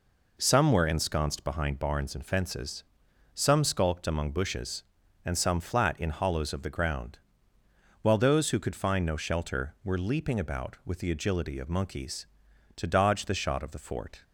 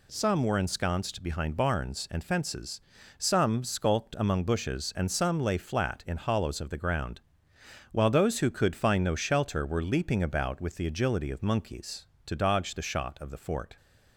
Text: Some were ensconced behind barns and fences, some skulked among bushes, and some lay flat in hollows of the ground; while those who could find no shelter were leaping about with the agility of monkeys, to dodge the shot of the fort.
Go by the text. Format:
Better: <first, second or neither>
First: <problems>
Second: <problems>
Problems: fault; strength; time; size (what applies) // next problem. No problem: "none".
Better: second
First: skips "lay"; at 5.5 s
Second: none